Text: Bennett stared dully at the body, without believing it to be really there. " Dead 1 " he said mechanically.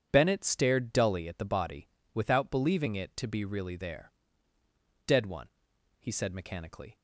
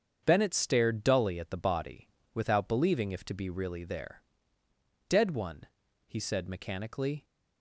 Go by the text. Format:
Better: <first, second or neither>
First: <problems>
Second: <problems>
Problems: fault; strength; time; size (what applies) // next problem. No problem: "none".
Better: first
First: starts louder than the rest; strong; until 1.1 s; 9.5 dB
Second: starts louder than the rest; strong; until 1.2 s; 8 dB // says "if" for "it"; at 3.1 s